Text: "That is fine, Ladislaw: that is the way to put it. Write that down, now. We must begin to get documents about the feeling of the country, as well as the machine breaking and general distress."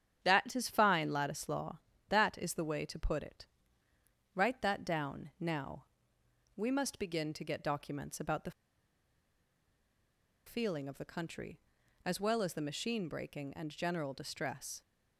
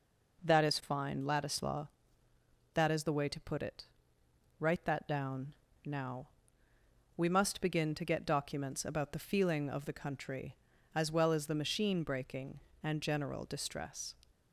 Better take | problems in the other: second | starts louder than the rest; strong; until 1.2 s; 9.5 dB // pauses between "the" and "feeling"; strong; at 8.5 s; 1.9 s long

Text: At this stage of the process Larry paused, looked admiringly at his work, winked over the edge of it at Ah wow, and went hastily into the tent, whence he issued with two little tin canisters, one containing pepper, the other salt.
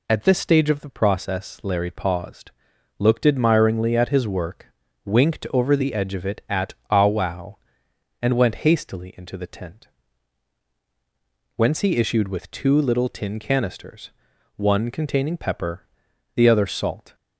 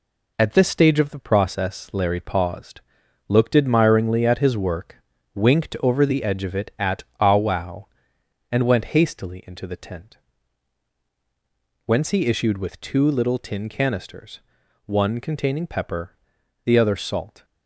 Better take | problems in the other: first | gets quieter; noticeable; throughout; 5.5 dB // pauses between "at" and "Ah"; slight; at 7.0 s; 0.16 s long; slight in the first

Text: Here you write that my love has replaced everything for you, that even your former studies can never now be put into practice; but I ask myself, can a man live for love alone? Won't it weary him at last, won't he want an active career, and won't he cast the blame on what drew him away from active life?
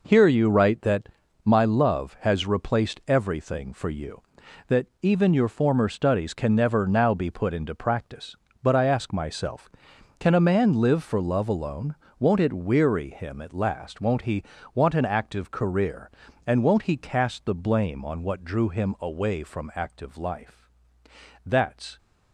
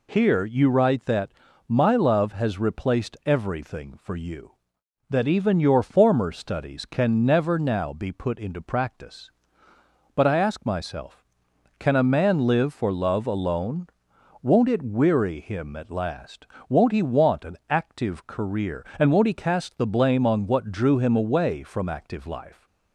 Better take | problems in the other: second | pauses between "that" and "my"; slight; at 1.0 s; 0.36 s long; also in the second // pauses between "that" and "even"; slight; at 4.8 s; 0.16 s long // pauses between "he" and "want"; slight; at 14.4 s; 0.32 s long // goes on to say "That's"; from 21.4 s on; 0.54 s long

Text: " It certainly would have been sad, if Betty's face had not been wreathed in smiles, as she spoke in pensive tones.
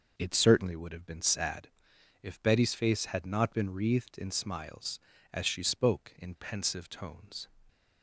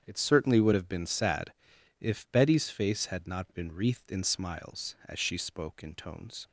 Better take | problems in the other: first | starts louder than the rest; strong; until 1.0 s; 8.5 dB // skips "pensive"; at 5.9 s

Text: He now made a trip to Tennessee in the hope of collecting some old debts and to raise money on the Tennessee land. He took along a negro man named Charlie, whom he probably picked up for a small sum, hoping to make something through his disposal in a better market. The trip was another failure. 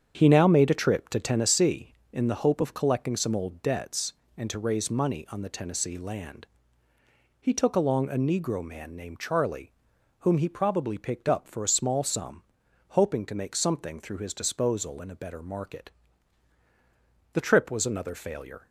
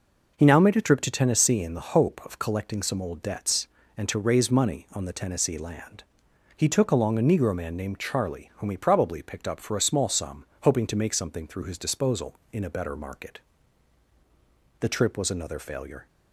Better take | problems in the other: second | starts louder than the rest; strong; until 1.6 s; 8 dB

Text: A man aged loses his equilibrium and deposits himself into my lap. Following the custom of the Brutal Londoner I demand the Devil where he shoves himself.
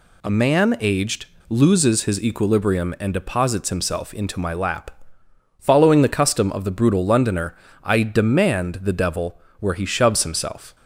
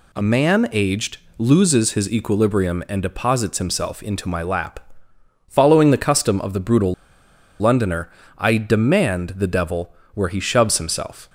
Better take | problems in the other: first | pauses between "aged" and "loses"; slight; at 1.1 s; 0.20 s long; slight in the first // pauses between "Brutal" and "Londoner"; noticeable; at 6.9 s; 0.65 s long // pauses between "Londoner" and "I"; slight; at 8.1 s; 0.26 s long; slight in the first // pauses between "Devil" and "where"; slight; at 9.9 s; 0.22 s long; slight in the first

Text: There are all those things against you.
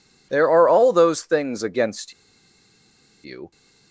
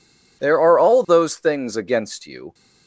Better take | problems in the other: second | pauses between "against" and "you"; at 2.1 s; 1.1 s long

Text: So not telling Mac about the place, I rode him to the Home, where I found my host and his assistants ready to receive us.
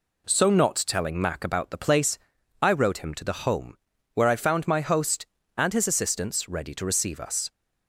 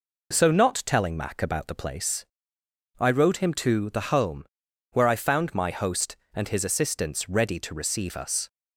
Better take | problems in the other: neither | none

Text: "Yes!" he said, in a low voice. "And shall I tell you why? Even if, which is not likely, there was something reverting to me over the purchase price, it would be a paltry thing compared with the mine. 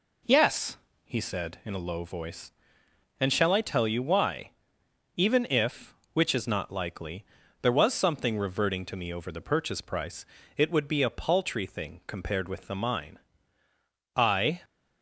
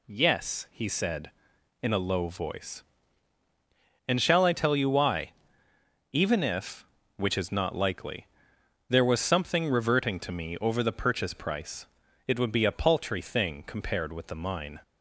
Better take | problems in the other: second | goes on to say "I"; slight; from 14.1 s on; 0.46 s long

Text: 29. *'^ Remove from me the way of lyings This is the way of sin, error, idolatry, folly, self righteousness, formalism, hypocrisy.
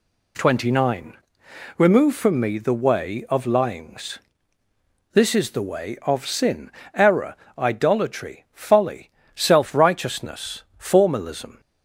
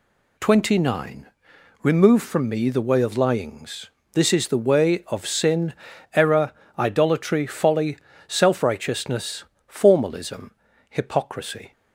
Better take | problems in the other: second | pauses between "lyings" and "This"; noticeable; at 4.1 s; 0.96 s long; slight in the second // stops before "hypocrisy"; at 11.5 s

